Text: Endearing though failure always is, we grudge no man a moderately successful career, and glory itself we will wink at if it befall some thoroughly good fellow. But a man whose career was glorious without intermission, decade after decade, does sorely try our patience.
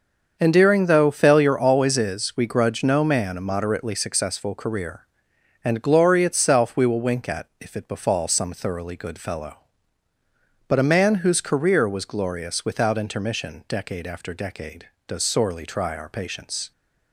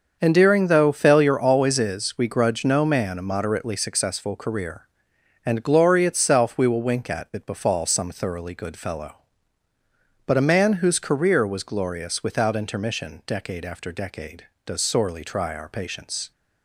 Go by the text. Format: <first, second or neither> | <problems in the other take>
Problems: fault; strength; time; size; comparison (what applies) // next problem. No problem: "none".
first | starts louder than the rest; until 1.2 s; 6.5 dB; also in the first // skips "if"; at 7.3 s